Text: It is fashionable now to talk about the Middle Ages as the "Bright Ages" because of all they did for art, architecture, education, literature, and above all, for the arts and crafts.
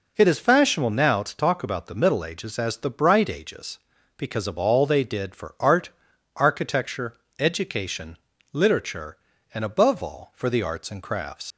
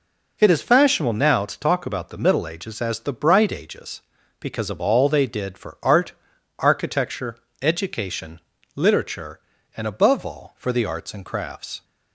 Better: second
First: leaves "crafts" unfinished; at 11.5 s; 105 ms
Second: none

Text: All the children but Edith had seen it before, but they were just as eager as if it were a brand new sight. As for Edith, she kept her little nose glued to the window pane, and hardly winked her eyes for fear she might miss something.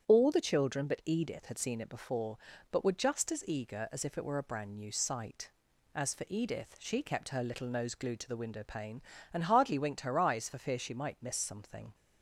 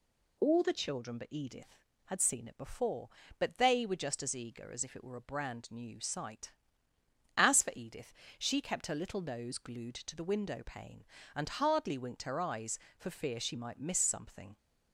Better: second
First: starts louder than the rest; strong; until 1.1 s; 9 dB // skips "they"; at 2.8 s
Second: none

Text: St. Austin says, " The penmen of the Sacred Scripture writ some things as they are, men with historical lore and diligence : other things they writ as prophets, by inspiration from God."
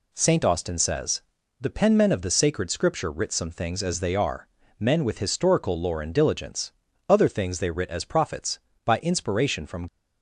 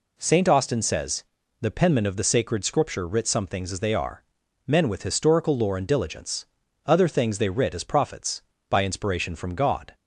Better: second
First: stops before "God"; at 9.8 s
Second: none

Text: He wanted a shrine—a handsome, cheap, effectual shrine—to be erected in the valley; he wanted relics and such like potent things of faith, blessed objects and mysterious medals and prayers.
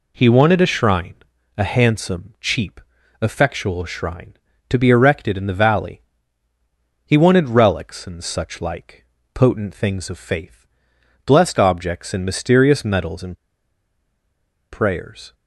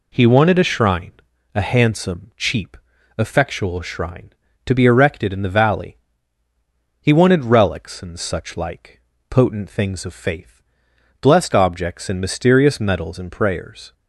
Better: second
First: pauses between "like" and "potent"; slight; at 9.0 s; 0.28 s long // pauses between "and" and "prayers"; strong; at 13.3 s; 1.3 s long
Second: pauses between "like" and "potent"; slight; at 9.0 s; 0.28 s long

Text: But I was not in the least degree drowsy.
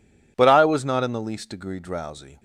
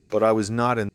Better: first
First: none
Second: stops before "the least degree drowsy"; at 0.8 s

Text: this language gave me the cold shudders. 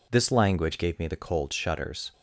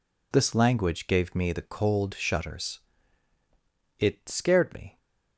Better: first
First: none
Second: goes on to say "It scared me"; noticeable; from 3.9 s on; 0.98 s long

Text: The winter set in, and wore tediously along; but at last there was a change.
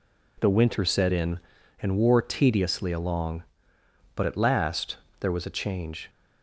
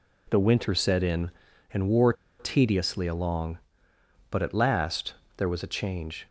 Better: first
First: pauses between "last" and "there"; slight; at 4.9 s; 0.24 s long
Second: pauses between "wore" and "tediously"; slight; at 2.1 s; 0.26 s long // pauses between "last" and "there"; slight; at 5.1 s; 0.24 s long

